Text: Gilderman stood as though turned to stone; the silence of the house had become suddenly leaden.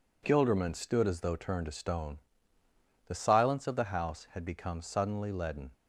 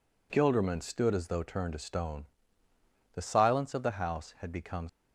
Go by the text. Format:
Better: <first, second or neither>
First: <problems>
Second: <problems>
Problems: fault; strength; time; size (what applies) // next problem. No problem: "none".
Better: first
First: none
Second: stops before "suddenly leaden"; at 4.8 s